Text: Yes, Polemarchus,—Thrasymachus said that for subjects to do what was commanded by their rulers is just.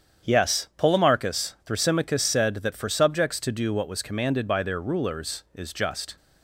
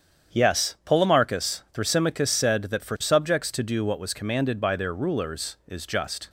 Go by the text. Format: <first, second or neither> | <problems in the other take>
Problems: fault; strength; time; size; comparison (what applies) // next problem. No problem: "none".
neither | starts louder than the rest; strong; the same in both